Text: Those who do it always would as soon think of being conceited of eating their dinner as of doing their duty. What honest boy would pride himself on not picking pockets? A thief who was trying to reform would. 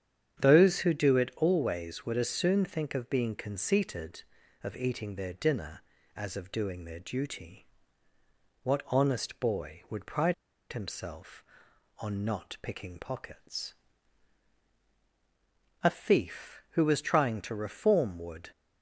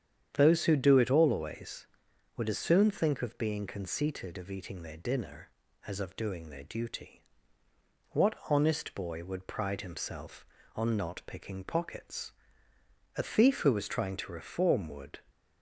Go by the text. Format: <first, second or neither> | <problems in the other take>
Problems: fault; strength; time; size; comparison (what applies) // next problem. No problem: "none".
second | starts louder than the rest; strong; until 1.4 s; 8.5 dB; strong in the second // pauses between "pride" and "himself"; at 10.3 s; 0.38 s long